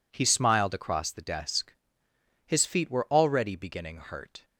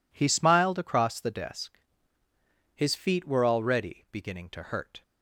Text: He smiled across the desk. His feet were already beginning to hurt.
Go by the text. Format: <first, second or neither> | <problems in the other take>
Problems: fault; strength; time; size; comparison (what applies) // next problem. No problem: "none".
second | skips "to"; at 3.9 s